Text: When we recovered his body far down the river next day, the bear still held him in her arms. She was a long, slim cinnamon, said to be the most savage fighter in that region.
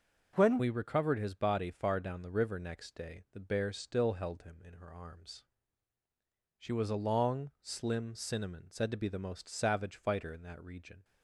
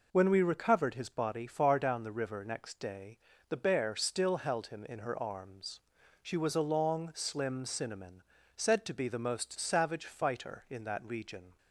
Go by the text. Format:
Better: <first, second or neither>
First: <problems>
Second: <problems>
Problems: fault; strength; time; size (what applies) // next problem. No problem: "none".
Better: second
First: changes voice at "we"; from 0.5 s on; 10.5 s long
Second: none